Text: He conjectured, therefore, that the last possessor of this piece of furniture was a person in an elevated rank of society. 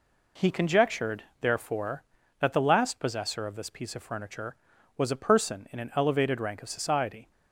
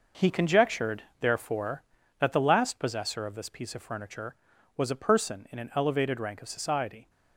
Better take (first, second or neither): first